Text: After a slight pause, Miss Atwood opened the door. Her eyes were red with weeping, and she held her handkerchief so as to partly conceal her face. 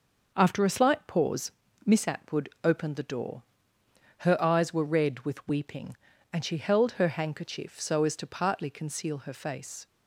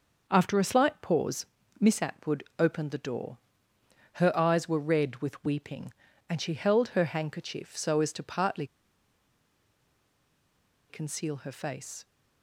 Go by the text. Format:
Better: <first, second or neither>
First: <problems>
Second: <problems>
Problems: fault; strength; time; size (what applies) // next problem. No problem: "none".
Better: first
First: starts louder than the rest; noticeable; until 1.3 s; 6 dB // pauses between "Atwood" and "opened"; slight; at 2.4 s; 0.15 s long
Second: starts louder than the rest; noticeable; until 1.3 s; 6 dB // pauses between "Atwood" and "opened"; slight; at 2.4 s; 0.16 s long // pauses between "partly" and "conceal"; strong; at 8.6 s; 2.2 s long